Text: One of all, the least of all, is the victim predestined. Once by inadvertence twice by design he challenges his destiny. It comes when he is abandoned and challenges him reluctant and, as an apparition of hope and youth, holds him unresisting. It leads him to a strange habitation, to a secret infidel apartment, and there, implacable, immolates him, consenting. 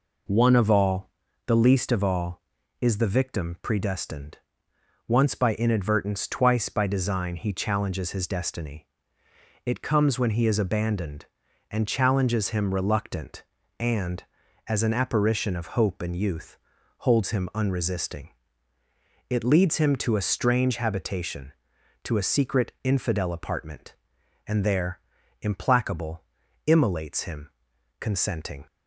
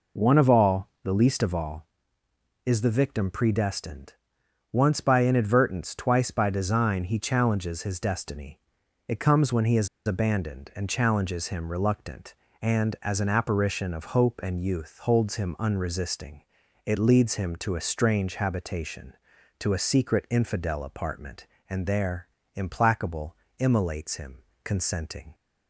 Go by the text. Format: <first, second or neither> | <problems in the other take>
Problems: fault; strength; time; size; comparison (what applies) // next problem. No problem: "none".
first | pauses between "is" and "abandoned"; slight; at 9.8 s; 0.20 s long